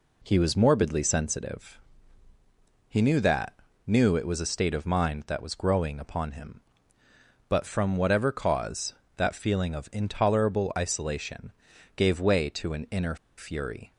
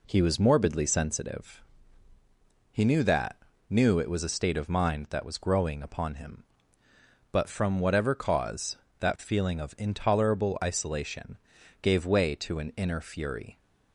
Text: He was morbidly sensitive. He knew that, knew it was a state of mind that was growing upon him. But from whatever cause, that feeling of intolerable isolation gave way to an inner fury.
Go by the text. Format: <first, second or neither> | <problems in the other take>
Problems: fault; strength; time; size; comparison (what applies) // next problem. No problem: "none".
second | pauses between "isolation" and "gave"; noticeable; at 11.5 s; 0.46 s long; noticeable in the second // pauses between "inner" and "fury"; slight; at 13.1 s; 0.20 s long